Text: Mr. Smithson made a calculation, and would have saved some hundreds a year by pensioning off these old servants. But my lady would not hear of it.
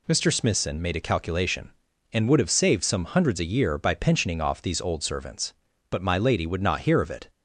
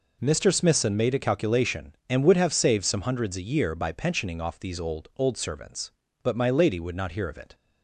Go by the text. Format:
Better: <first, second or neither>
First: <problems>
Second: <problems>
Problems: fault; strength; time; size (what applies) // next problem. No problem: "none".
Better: first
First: none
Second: says "old" twice; at 5.1 s